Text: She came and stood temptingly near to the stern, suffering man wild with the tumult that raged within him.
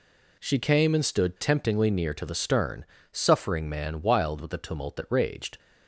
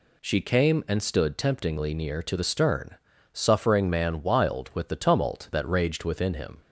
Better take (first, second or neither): second